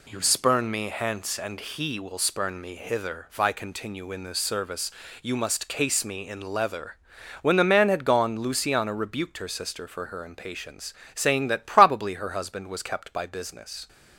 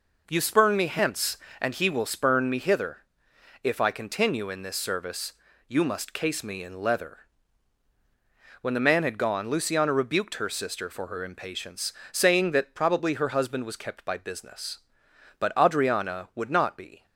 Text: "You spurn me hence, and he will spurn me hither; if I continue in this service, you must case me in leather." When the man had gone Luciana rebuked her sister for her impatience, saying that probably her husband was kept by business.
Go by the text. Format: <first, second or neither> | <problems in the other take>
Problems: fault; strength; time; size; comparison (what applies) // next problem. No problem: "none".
first | goes on to say "But Adriana would not be"; strong; from 15.3 s on; 1.6 s long